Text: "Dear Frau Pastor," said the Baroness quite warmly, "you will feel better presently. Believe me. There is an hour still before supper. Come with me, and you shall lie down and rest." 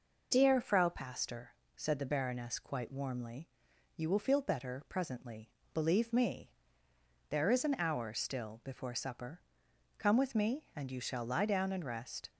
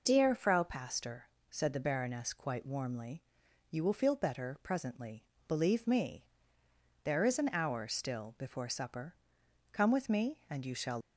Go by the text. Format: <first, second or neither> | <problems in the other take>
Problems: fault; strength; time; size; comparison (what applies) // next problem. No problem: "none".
first | stops before "lie down and rest"; at 11.0 s